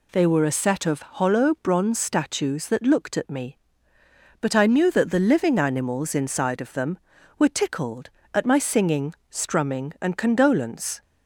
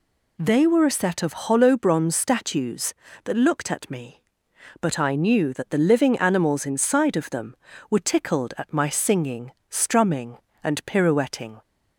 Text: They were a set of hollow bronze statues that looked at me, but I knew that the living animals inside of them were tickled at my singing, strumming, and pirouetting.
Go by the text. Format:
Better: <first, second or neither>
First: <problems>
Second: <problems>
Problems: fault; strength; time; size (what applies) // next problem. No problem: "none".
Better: second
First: says "condolence" for "pirouetting"; at 10.1 s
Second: none